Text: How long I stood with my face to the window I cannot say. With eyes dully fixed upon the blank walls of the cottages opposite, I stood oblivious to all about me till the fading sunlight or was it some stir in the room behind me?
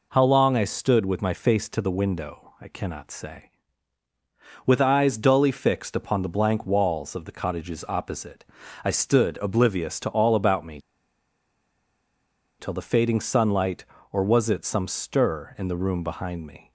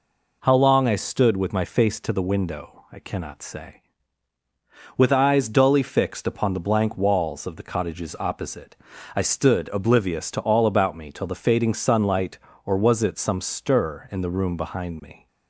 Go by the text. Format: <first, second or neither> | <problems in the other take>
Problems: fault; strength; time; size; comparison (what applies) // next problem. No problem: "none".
second | pauses between "me" and "till"; strong; at 10.7 s; 1.7 s long